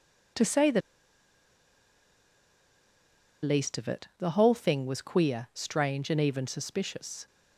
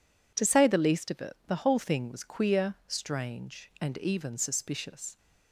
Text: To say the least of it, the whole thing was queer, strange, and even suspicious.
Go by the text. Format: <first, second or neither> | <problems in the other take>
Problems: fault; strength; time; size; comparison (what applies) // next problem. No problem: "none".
second | pauses between "the" and "least"; strong; at 0.8 s; 2.6 s long